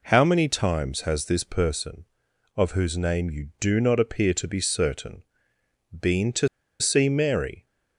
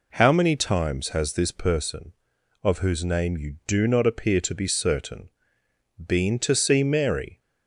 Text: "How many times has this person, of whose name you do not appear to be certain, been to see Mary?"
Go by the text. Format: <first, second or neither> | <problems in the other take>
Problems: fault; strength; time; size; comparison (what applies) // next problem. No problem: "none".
second | pauses between "to" and "see"; slight; at 6.4 s; 0.33 s long